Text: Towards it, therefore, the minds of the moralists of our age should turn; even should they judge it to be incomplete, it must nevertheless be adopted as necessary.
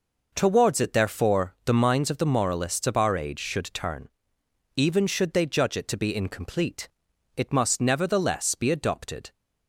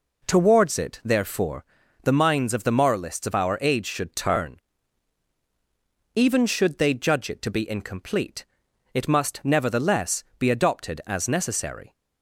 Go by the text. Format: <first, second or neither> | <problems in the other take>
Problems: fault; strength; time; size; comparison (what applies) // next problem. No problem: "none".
second | stops before "as necessary"; at 9.3 s